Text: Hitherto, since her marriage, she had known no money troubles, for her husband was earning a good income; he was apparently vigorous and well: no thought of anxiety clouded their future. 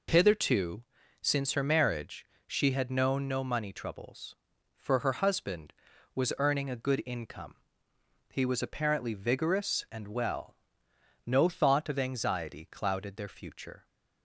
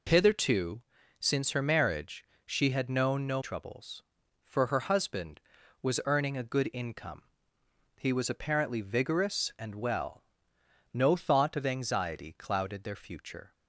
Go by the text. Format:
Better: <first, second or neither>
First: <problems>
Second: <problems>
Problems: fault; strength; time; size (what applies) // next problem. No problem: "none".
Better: first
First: none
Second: skips "money"; at 3.4 s